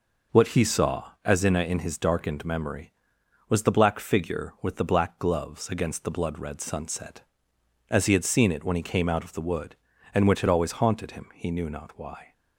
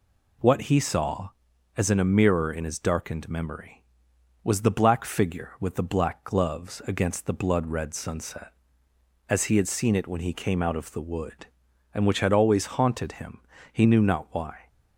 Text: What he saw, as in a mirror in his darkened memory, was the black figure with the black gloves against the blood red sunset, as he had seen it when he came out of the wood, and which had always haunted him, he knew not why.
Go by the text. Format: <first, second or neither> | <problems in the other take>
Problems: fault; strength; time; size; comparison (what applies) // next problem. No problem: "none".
second | skips "mirror"; at 1.6 s